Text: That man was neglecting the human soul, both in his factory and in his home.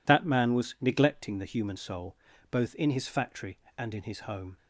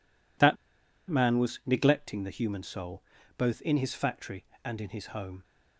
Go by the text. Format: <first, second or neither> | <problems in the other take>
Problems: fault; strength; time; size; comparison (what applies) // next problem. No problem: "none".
first | pauses between "That" and "man"; noticeable; at 0.5 s; 0.53 s long